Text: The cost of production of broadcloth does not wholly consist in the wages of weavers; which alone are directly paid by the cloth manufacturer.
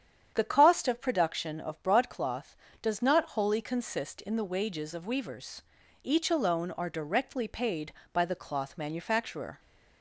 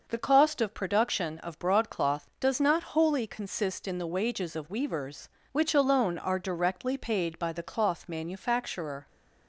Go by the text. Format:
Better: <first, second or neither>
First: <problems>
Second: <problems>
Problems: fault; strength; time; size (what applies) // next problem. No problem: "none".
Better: second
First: starts louder than the rest; strong; until 1.3 s; 8.5 dB // says "each" for "which"; at 6.0 s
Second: starts louder than the rest; noticeable; until 1.0 s; 6 dB